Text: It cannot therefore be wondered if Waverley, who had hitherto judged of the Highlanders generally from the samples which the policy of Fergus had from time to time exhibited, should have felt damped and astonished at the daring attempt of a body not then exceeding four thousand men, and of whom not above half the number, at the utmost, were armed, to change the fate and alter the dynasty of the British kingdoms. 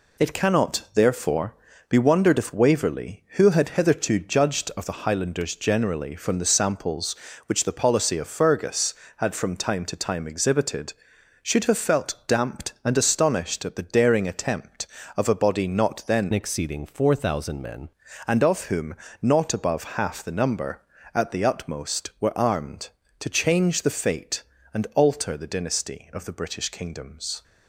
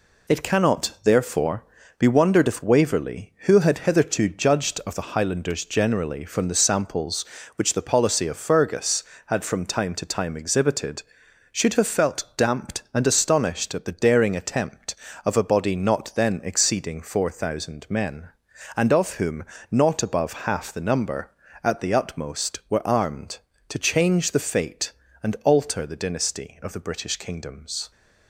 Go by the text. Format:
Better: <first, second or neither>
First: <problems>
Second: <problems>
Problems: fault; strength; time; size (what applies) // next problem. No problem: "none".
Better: second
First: pauses between "therefore" and "be"; slight; at 1.5 s; 0.34 s long // changes voice from "exceeding" to "men"; from 16.3 to 17.8 s; 1.5 s long // pauses between "whom" and "not"; slight; at 18.9 s; 0.26 s long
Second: pauses between "therefore" and "be"; slight; at 1.6 s; 0.34 s long // pauses between "whom" and "not"; slight; at 19.4 s; 0.26 s long